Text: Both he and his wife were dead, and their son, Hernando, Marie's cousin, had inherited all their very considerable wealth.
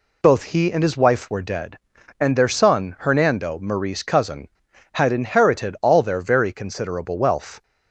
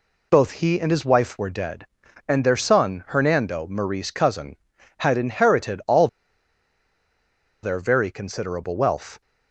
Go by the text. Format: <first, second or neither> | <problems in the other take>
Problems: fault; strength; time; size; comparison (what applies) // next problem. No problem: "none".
first | pauses between "all" and "their"; strong; at 6.0 s; 1.5 s long